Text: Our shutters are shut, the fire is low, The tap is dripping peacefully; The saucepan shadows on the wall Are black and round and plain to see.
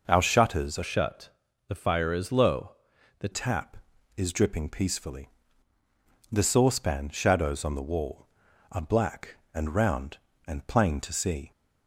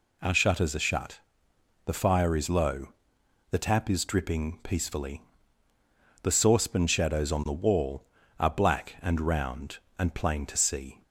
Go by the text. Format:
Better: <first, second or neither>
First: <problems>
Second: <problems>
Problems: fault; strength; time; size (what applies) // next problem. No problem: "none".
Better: second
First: changes voice from "shut" to "The"; from 0.8 to 3.2 s; 2.4 s long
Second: none